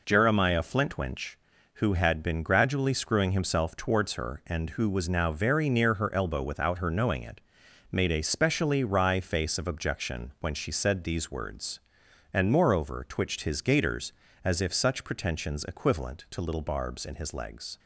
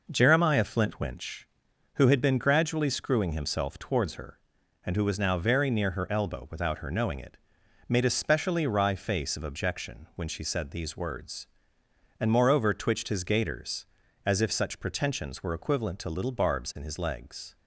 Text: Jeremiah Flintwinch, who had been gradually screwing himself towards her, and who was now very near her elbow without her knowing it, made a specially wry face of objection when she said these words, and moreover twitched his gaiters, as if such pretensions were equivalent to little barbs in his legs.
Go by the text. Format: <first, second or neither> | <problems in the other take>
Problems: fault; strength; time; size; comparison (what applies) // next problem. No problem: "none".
second | skips "were"; at 15.6 s